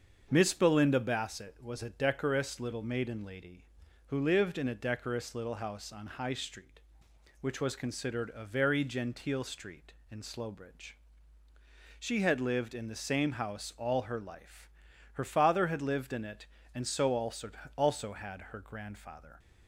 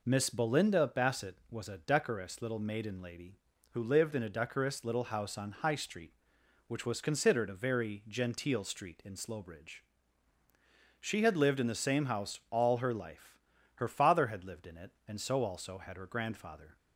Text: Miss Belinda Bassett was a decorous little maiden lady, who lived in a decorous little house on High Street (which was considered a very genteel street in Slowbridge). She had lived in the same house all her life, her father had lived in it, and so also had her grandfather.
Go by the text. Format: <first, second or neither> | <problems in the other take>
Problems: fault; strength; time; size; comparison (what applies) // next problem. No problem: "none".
second | starts louder than the rest; until 1.3 s; 6.5 dB // says "also" twice; at 17.7 s